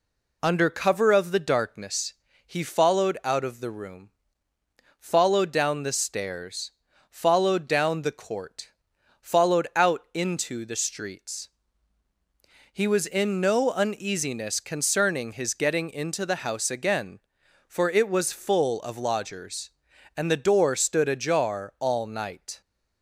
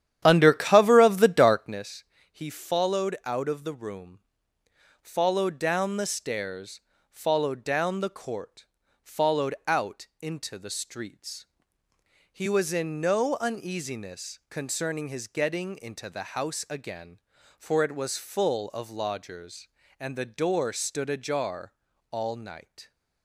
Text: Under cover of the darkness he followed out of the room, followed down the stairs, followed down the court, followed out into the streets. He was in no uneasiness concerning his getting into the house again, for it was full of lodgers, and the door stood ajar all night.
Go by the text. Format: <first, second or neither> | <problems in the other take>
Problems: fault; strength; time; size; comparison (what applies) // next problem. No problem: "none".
first | starts louder than the rest; strong; until 1.9 s; 10.5 dB // pauses between "darkness" and "he"; slight; at 2.0 s; 0.28 s long; slight in the first // pauses between "ajar" and "all"; at 21.7 s; 0.40 s long